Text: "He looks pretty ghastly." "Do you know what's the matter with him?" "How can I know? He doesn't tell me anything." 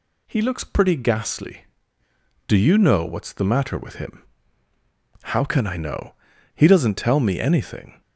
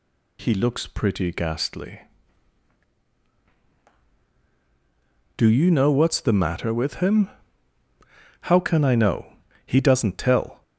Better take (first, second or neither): first